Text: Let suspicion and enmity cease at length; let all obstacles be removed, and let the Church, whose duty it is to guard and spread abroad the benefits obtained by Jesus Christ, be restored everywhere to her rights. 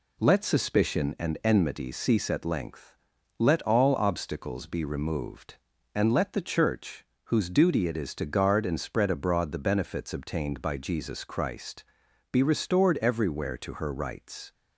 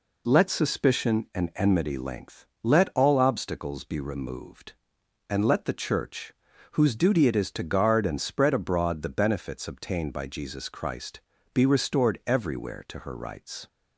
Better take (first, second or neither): first